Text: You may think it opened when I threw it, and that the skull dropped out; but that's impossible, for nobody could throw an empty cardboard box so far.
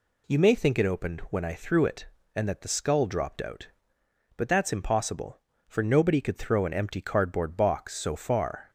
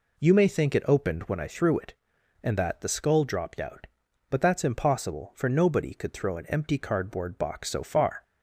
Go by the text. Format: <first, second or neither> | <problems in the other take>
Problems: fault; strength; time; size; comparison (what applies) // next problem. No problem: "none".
neither | none